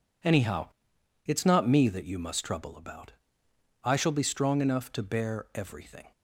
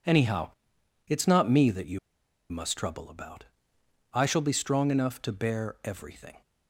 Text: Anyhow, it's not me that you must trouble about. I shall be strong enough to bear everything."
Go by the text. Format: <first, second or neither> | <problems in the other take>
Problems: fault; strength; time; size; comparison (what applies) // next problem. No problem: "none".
first | pauses between "you" and "must"; noticeable; at 1.9 s; 0.52 s long